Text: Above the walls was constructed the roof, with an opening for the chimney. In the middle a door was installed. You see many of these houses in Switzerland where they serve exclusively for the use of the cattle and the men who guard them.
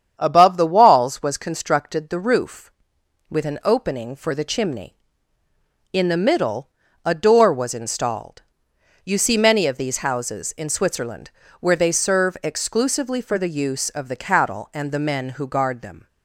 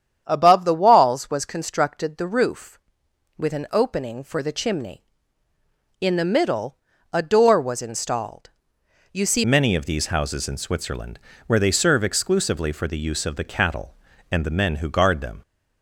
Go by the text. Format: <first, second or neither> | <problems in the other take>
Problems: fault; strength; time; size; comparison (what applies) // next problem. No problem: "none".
first | starts louder than the rest; strong; until 1.2 s; 9 dB; strong in the first // pauses between "middle" and "a"; slight; at 6.7 s; 0.36 s long; slight in the first // changes voice at "many"; from 9.4 s on; 6.0 s long // pauses between "Switzerland" and "where"; slight; at 11.1 s; 0.26 s long; slight in the first